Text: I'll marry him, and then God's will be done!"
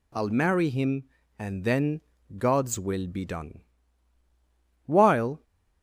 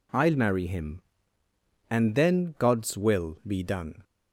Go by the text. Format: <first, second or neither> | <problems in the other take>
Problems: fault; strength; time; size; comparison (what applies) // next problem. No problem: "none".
second | pauses between "then" and "God's"; slight; at 2.0 s; 0.36 s long // goes on to say "While"; from 4.8 s on; 0.58 s long